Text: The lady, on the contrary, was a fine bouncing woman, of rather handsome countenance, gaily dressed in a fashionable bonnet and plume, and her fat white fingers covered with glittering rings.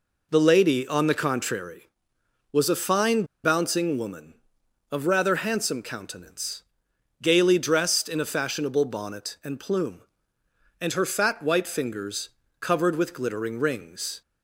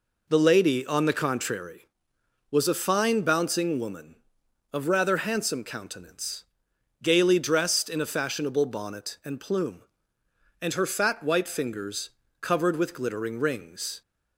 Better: second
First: pauses between "fine" and "bouncing"; slight; at 3.2 s; 0.19 s long // pauses between "fingers" and "covered"; slight; at 12.2 s; 0.32 s long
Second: pauses between "fingers" and "covered"; slight; at 12.0 s; 0.32 s long

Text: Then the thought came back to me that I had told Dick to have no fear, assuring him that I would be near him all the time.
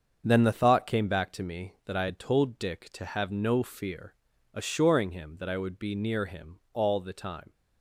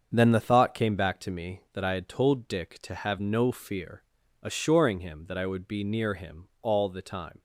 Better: neither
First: starts louder than the rest; until 1.2 s; 7 dB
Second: starts louder than the rest; until 1.1 s; 7 dB

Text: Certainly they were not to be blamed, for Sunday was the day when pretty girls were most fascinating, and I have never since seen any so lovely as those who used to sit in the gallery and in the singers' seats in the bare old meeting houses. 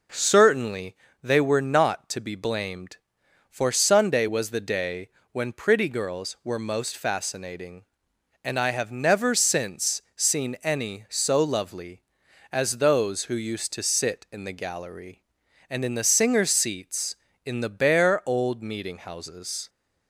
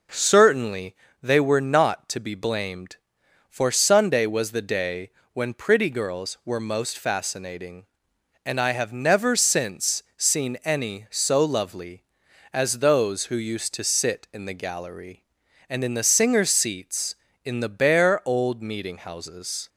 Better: neither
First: pauses between "Certainly" and "they"; slight; at 0.9 s; 0.26 s long // pauses between "day" and "when"; slight; at 5.0 s; 0.24 s long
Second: pauses between "Certainly" and "they"; slight; at 0.9 s; 0.26 s long // pauses between "day" and "when"; slight; at 5.0 s; 0.24 s long

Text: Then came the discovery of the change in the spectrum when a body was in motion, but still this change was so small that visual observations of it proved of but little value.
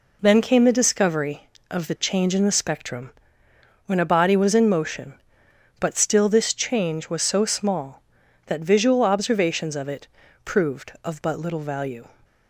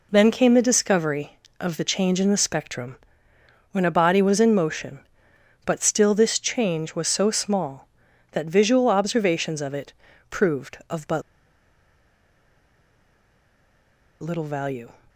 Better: first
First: pauses between "spectrum" and "when"; noticeable; at 3.1 s; 0.76 s long // pauses between "it" and "proved"; at 10.0 s; 0.38 s long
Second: pauses between "spectrum" and "when"; noticeable; at 2.9 s; 0.76 s long // pauses between "it" and "proved"; at 9.9 s; 0.38 s long // pauses between "but" and "little"; strong; at 11.2 s; 3.0 s long

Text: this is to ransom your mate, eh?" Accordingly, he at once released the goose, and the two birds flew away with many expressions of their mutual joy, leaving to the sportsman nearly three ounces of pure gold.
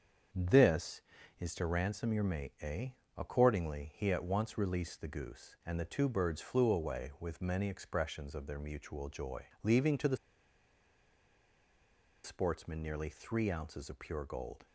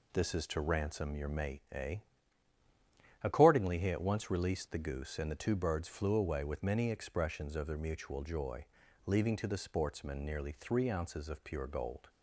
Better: second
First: starts louder than the rest; strong; until 1.7 s; 7.5 dB // pauses between "the" and "sportsman"; strong; at 10.1 s; 2.0 s long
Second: none

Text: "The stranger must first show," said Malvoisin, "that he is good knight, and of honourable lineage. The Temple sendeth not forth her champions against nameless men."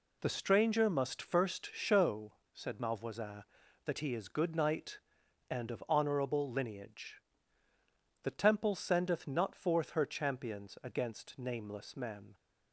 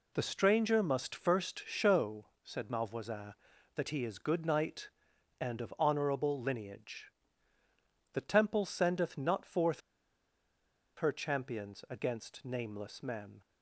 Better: first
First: none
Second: pauses between "forth" and "her"; at 9.8 s; 1.1 s long

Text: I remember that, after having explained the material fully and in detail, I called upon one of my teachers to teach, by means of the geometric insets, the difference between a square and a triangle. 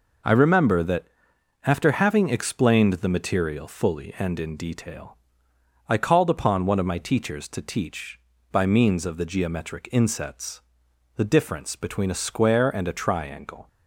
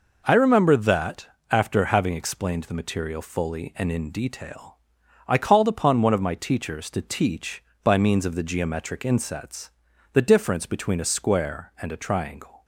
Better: neither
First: none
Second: none

